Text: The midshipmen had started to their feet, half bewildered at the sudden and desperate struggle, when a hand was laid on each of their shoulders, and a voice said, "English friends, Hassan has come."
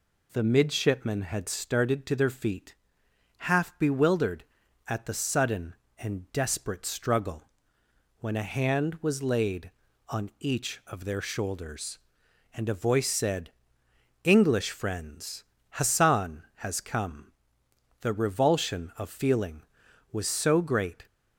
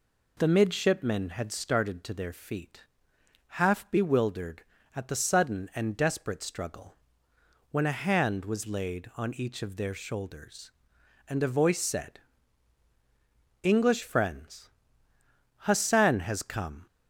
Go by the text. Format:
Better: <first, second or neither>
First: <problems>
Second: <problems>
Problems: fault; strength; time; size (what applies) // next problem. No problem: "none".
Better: second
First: goes on to say "The revulsion of feeling was so great"; strong; from 18.0 s on; 3.0 s long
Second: none